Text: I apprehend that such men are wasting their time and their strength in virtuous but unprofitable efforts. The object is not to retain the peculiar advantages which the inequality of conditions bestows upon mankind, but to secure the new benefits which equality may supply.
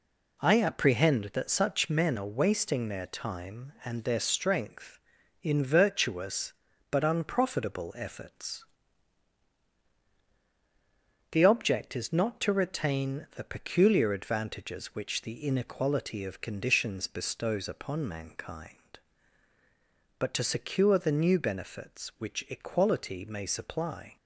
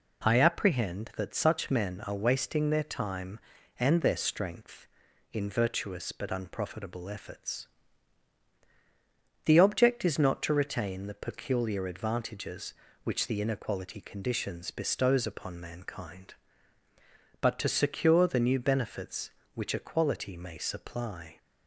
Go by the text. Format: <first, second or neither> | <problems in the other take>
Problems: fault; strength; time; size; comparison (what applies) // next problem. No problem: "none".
first | skips "of"; at 13.9 s